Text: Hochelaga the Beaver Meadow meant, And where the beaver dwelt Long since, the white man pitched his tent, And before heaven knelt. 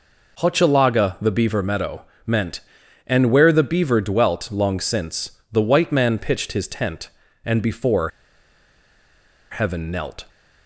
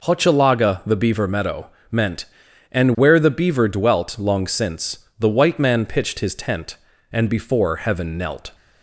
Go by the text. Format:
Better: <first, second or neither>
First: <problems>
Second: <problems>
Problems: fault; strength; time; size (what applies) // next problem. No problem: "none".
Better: second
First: pauses between "Meadow" and "meant"; slight; at 2.0 s; 0.22 s long // pauses between "before" and "heaven"; strong; at 8.0 s; 1.4 s long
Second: pauses between "Meadow" and "meant"; slight; at 1.6 s; 0.22 s long